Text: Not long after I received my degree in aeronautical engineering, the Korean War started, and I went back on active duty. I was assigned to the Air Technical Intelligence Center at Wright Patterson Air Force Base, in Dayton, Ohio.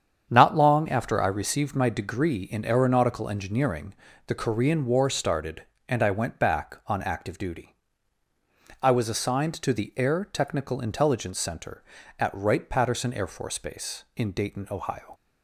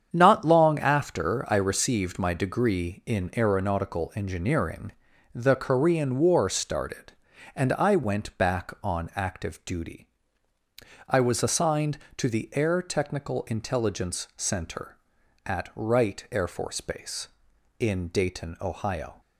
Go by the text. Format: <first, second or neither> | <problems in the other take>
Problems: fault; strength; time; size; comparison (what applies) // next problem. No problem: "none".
first | starts louder than the rest; strong; until 1.1 s; 8 dB; strong in the first // skips "Patterson"; at 16.2 s